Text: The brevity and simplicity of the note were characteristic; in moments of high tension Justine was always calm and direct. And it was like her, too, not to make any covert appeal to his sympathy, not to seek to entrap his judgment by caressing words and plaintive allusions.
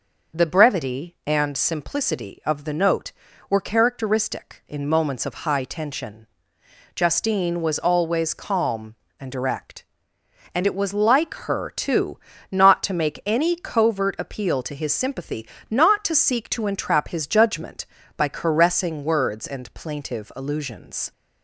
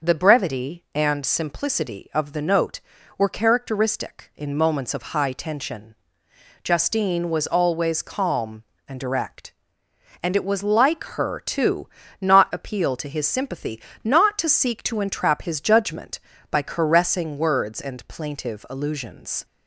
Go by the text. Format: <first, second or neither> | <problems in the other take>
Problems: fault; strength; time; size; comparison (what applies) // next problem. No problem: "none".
first | pauses between "tension" and "Justine"; noticeable; at 5.9 s; 0.70 s long; noticeable in the first // skips "to make any covert"; at 12.5 s